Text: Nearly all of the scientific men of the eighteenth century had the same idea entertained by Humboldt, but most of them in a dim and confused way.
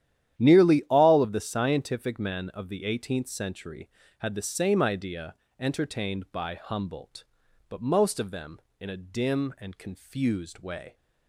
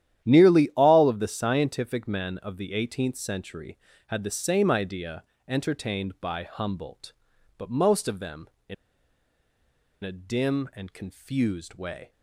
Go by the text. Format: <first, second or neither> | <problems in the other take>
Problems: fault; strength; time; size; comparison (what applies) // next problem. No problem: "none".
first | starts louder than the rest; strong; until 1.3 s; 11 dB; strong in the first // pauses between "idea" and "entertained"; slight; at 5.2 s; 0.26 s long; slight in the first // pauses between "in" and "a"; strong; at 8.7 s; 1.2 s long